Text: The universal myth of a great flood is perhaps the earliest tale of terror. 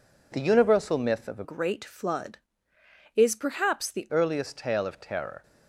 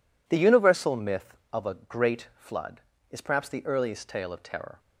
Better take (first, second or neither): second